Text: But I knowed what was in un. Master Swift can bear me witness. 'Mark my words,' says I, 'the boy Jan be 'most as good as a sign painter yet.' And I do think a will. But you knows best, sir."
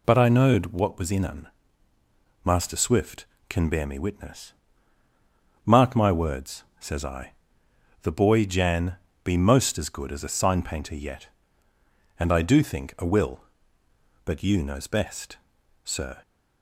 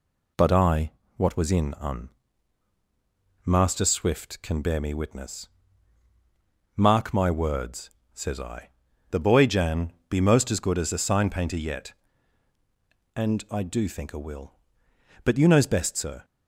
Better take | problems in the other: first | skips "knowed"; at 1.0 s // pauses between "Jan" and "be"; slight; at 9.9 s; 0.16 s long; slight in the first

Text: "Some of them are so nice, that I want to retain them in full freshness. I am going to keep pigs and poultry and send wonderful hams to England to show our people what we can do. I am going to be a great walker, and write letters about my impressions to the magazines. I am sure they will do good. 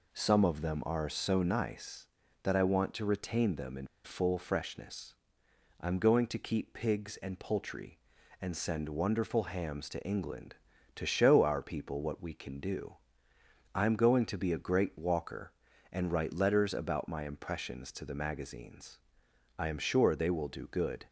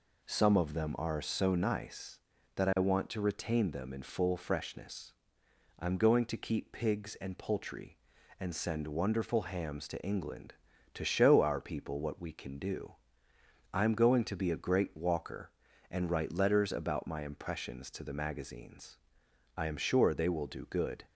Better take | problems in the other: second | pauses between "in" and "full"; slight; at 3.8 s; 0.17 s long

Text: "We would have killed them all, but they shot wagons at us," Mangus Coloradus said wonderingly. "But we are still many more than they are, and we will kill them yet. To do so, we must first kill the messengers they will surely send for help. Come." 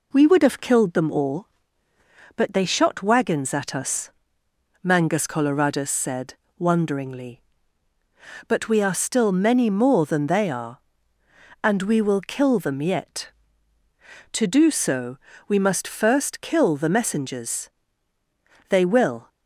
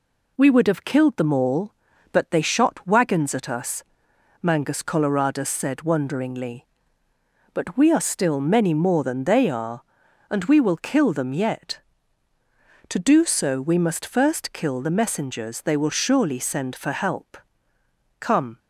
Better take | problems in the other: second | pauses between "said" and "wonderingly"; slight; at 6.3 s; 0.22 s long // pauses between "messengers" and "they"; at 17.7 s; 1.0 s long // stops before "surely send for help Come"; at 19.2 s

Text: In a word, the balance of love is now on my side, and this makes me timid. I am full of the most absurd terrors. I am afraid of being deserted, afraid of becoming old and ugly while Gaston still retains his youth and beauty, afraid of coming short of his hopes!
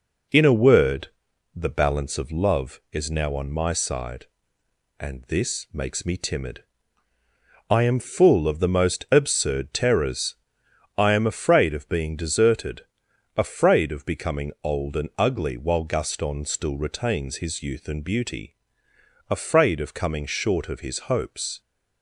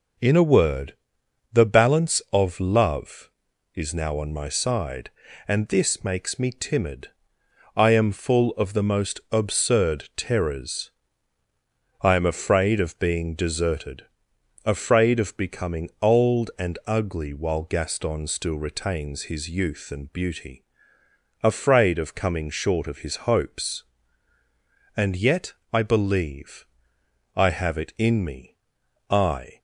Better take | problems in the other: first | goes on to say "And yet I believe I have it in me I"; strong; from 24.9 s on; 4.6 s long

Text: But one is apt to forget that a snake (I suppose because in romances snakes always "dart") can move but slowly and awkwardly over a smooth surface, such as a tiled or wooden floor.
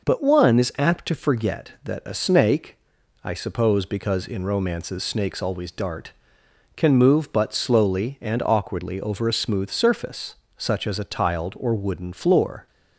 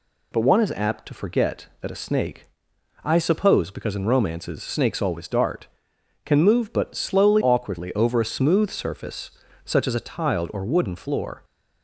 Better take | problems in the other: first | skips "and"; at 7.4 s

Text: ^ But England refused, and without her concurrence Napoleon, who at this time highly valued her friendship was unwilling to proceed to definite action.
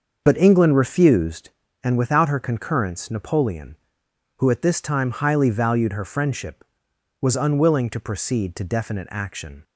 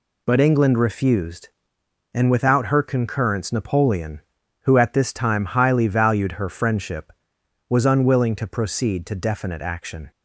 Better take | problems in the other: second | starts louder than the rest; until 1.5 s; 6.5 dB

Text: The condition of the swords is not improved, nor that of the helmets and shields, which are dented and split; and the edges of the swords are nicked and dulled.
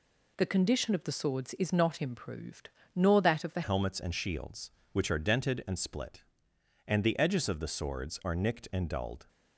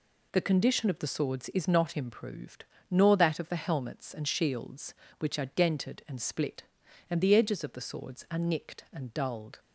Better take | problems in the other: second | changes voice at "helmets"; from 3.6 s on; 5.6 s long

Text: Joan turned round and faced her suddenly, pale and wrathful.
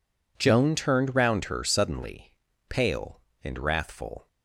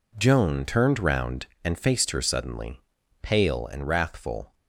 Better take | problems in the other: second | skips "and faced"; at 1.4 s

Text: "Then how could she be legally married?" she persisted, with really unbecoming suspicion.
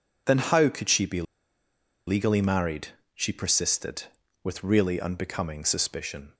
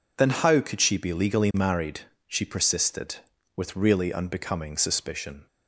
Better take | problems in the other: second | pauses between "be" and "legally"; noticeable; at 1.2 s; 0.84 s long

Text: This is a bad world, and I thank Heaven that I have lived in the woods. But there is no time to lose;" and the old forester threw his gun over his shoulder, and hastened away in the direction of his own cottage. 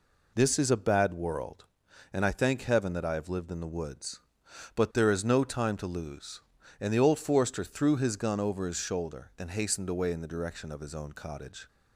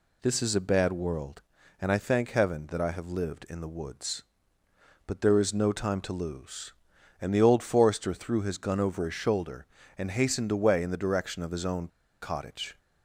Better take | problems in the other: first | pauses between "own" and "cottage"; slight; at 11.8 s; 0.34 s long

